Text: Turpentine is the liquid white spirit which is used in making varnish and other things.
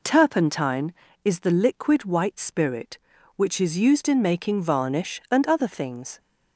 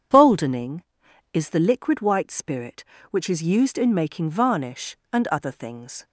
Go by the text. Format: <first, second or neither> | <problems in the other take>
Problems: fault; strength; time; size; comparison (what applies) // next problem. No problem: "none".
first | starts louder than the rest; strong; until 1.6 s; 8 dB // says "Boldening" for "Turpentine"; at 0.1 s